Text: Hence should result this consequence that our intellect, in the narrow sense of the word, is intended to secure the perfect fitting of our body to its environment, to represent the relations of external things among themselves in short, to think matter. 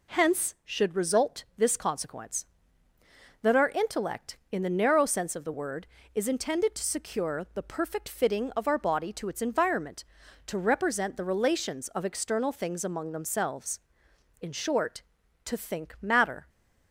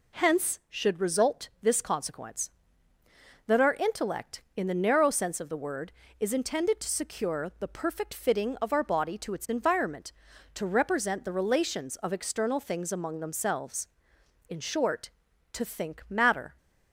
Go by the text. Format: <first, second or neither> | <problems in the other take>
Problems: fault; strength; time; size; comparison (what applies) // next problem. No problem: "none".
neither | none